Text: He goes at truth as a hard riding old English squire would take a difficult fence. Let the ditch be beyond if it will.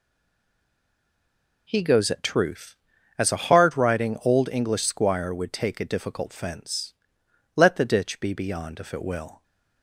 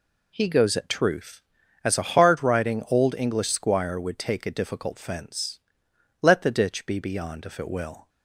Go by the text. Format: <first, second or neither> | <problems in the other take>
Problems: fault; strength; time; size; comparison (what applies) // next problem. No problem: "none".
second | stays silent before the first word; noticeable; until 1.6 s; 1.6 s long